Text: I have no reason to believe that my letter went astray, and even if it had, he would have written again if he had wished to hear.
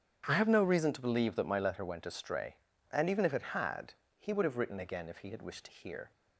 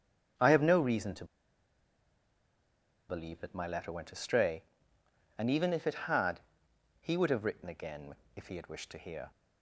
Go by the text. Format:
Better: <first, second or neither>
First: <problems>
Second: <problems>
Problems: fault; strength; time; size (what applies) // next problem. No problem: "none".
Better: first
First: starts louder than the rest; strong; until 1.2 s; 8.5 dB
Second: starts louder than the rest; strong; until 3.2 s; 7.5 dB // pauses between "to" and "believe"; strong; at 1.2 s; 1.8 s long // pauses between "again" and "if"; slight; at 8.1 s; 0.20 s long